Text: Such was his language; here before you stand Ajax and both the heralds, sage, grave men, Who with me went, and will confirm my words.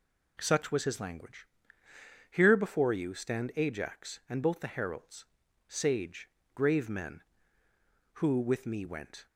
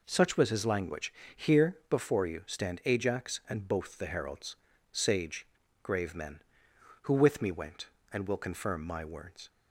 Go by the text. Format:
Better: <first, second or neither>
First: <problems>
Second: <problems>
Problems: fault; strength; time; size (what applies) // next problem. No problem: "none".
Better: second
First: stops before "and will confirm my words"; at 9.2 s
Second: none